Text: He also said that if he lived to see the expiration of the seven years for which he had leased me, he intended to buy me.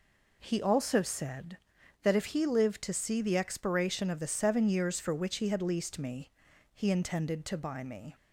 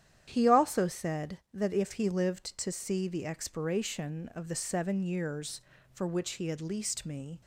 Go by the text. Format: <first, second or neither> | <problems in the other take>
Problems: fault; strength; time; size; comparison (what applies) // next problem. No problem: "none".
first | starts louder than the rest; strong; until 1.3 s; 10 dB // stops before "he intended to buy me"; at 7.4 s